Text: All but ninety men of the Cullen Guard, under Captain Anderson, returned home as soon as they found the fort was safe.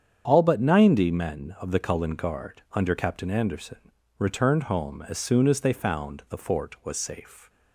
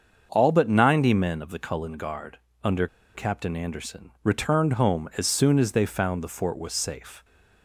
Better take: first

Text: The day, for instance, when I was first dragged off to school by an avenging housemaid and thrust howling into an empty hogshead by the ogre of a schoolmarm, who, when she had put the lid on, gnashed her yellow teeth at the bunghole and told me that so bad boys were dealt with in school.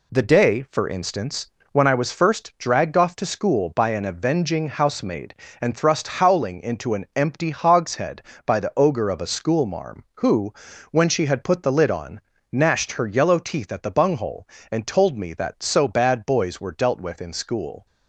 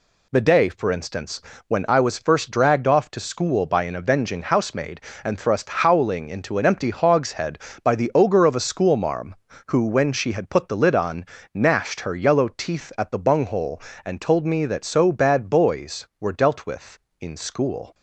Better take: neither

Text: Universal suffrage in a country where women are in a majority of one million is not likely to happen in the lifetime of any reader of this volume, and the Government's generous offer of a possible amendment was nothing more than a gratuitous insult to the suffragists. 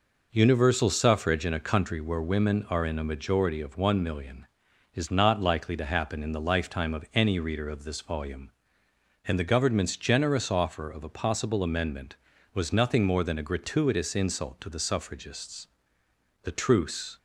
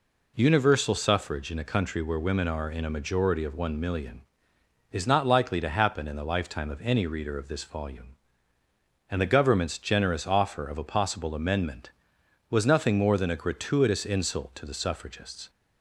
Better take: second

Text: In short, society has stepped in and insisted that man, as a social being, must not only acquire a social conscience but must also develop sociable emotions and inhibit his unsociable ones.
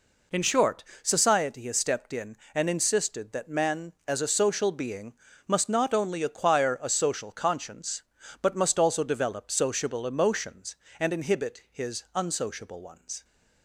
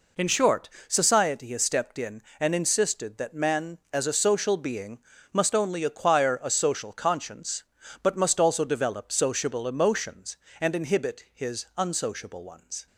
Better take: first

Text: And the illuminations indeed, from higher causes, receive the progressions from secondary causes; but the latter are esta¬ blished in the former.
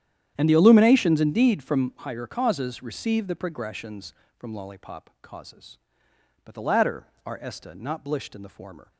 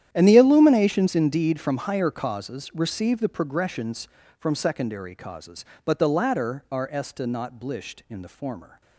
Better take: second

